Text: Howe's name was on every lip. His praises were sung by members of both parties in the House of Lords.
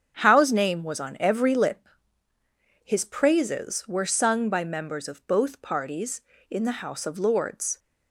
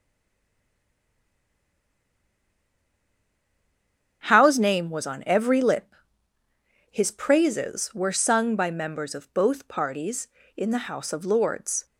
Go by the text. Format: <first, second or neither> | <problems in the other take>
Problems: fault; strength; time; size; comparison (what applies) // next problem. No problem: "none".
first | stays silent before the first word; strong; until 4.2 s; 4.2 s long // starts louder than the rest; strong; until 5.2 s; 7.5 dB; strong in the first